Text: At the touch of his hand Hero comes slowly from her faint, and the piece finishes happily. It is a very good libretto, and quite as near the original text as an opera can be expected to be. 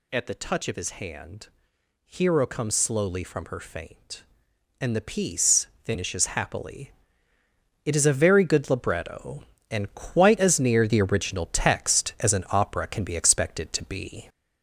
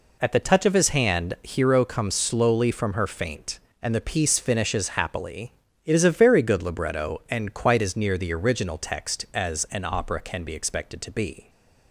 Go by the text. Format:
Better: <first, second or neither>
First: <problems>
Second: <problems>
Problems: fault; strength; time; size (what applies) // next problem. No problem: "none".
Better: second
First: gets louder; throughout; 4 dB // pauses between "hand" and "Hero"; noticeable; at 1.4 s; 0.58 s long // pauses between "piece" and "finishes"; slight; at 5.6 s; 0.18 s long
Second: none